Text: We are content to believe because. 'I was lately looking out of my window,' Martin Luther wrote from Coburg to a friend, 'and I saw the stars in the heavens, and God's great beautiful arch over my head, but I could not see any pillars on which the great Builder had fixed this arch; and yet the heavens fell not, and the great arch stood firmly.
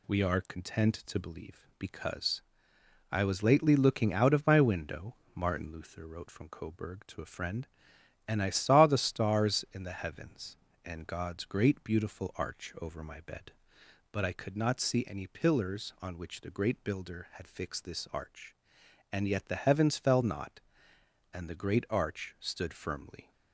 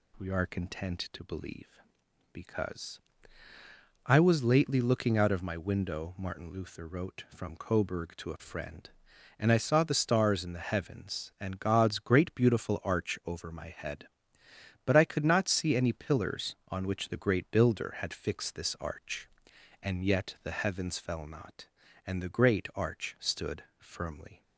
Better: second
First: says "bed" for "head"; at 13.2 s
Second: none

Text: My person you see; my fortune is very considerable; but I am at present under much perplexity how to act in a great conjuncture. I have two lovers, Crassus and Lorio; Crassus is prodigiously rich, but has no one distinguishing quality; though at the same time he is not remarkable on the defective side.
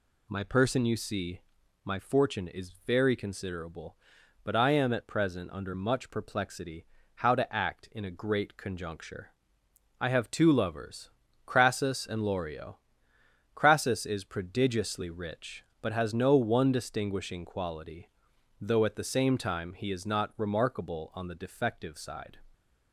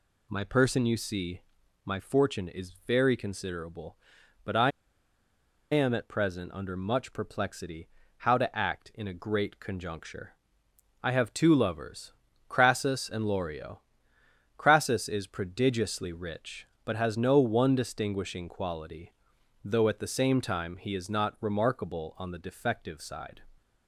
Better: first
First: pauses between "perplexity" and "how"; slight; at 6.8 s; 0.30 s long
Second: pauses between "I" and "am"; at 4.7 s; 1.0 s long // pauses between "perplexity" and "how"; slight; at 7.8 s; 0.30 s long

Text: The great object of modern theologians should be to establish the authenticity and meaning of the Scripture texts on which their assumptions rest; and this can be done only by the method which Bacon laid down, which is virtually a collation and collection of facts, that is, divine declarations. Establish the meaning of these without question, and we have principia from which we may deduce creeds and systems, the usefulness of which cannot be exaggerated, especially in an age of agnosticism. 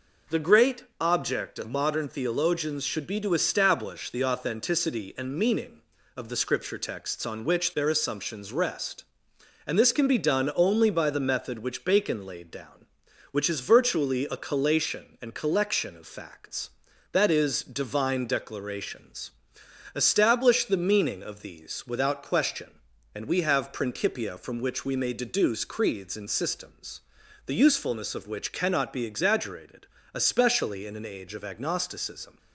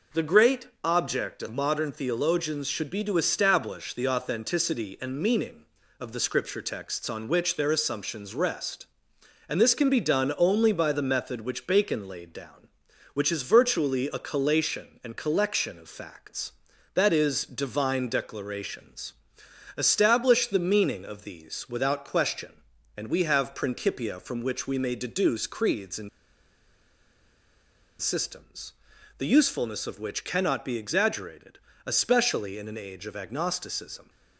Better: first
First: pauses between "great" and "object"; slight; at 0.8 s; 0.18 s long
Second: pauses between "great" and "object"; slight; at 0.6 s; 0.18 s long // pauses between "and" and "systems"; strong; at 26.0 s; 1.9 s long

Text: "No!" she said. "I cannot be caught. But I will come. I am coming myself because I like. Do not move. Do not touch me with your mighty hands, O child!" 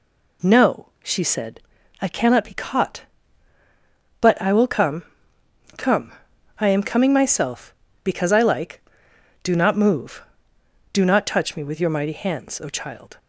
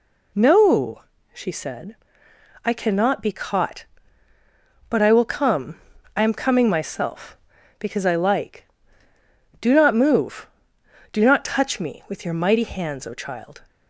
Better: second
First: says "come" twice; at 5.7 s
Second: none

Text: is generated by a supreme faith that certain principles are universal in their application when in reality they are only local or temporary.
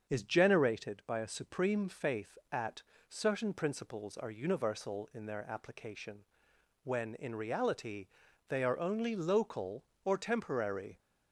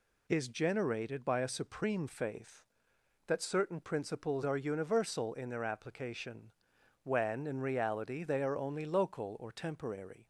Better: second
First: starts louder than the rest; until 1.1 s; 7 dB // says "at" for "that"; at 2.5 s // pauses between "application" and "when"; noticeable; at 6.2 s; 0.64 s long // pauses between "reality" and "they"; at 8.0 s; 0.42 s long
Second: pauses between "application" and "when"; noticeable; at 6.5 s; 0.52 s long

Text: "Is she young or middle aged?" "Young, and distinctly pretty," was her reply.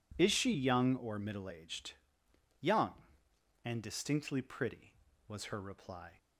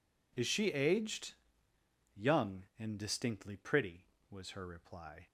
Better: first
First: none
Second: skips "young or middle"; at 0.7 s

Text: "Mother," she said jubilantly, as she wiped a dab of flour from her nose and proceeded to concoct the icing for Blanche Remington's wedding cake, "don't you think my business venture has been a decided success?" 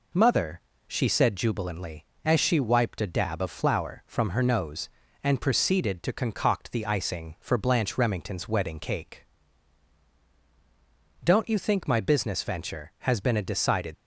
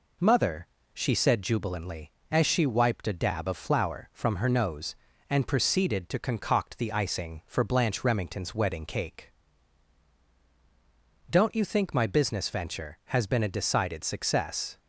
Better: second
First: stops before "success"; at 13.9 s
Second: none

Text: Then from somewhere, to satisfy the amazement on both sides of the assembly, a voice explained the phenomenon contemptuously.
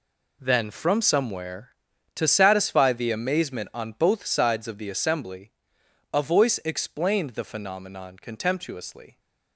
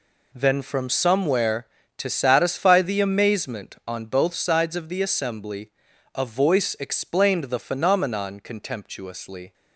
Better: neither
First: none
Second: none

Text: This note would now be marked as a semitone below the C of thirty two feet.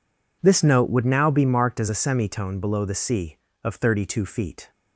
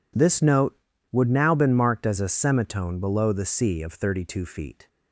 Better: first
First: none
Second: says "been" for "be"; at 1.5 s

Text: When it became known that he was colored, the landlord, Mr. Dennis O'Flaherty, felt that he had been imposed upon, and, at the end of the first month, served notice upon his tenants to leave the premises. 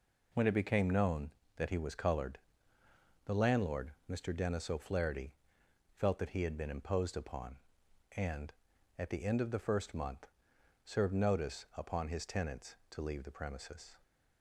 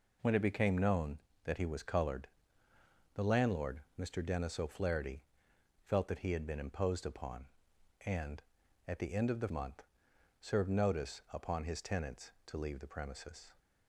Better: first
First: none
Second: skips "first"; at 9.4 s

